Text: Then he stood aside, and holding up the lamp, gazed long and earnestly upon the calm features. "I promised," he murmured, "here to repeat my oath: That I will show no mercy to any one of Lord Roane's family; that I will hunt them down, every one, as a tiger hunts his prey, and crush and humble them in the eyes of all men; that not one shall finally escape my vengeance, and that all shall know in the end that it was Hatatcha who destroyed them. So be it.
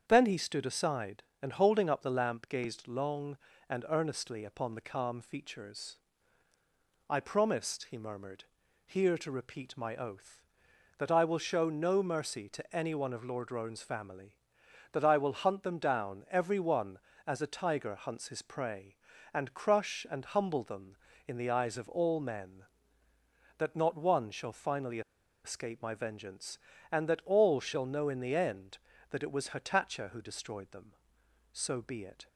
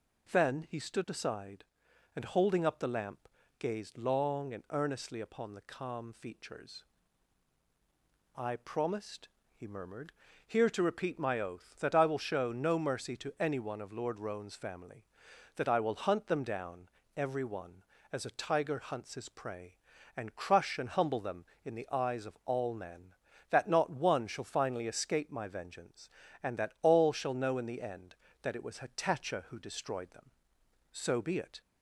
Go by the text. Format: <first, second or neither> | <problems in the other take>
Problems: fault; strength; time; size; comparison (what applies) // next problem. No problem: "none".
second | starts louder than the rest; strong; until 1.0 s; 7.5 dB // pauses between "finally" and "escape"; at 25.0 s; 0.44 s long